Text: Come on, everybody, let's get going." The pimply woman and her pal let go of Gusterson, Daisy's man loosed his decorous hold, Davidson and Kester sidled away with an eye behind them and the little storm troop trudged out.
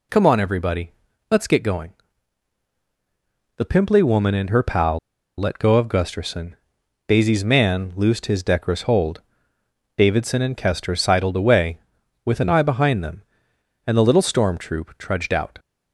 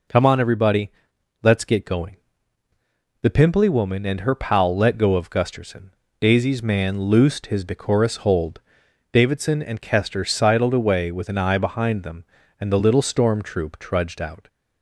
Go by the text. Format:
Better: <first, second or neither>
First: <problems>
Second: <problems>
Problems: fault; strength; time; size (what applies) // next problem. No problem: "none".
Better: second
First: pauses between "pal" and "let"; at 4.9 s; 0.39 s long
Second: none